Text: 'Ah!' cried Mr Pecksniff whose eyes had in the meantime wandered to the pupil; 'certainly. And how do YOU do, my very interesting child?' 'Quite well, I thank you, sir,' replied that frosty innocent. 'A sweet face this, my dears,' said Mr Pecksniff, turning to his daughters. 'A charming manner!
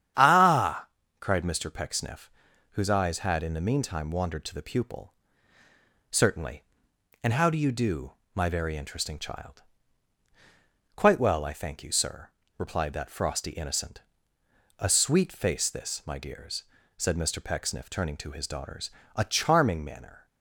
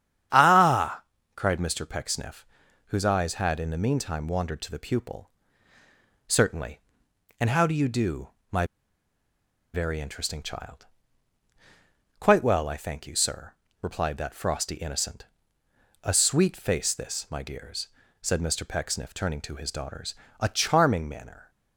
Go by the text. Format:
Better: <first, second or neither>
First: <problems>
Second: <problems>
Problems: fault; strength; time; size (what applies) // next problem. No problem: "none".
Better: first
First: starts louder than the rest; strong; until 1.4 s; 9 dB // pauses between "Pecksniff" and "whose"; at 2.3 s; 0.44 s long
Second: starts louder than the rest; strong; until 1.6 s; 9 dB // pauses between "Pecksniff" and "whose"; at 2.4 s; 0.44 s long // pauses between "my" and "very"; at 8.6 s; 1.0 s long